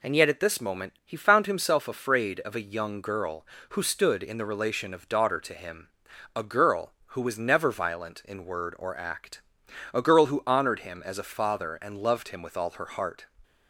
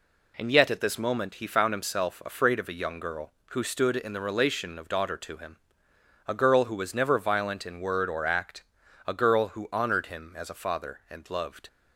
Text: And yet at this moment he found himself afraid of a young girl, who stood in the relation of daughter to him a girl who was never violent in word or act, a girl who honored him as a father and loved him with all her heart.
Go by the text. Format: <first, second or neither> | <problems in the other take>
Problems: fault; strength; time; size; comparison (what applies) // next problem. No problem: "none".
first | pauses between "him" and "a"; noticeable; at 5.5 s; 0.68 s long; noticeable in the first // stops before "him with all her heart"; at 11.6 s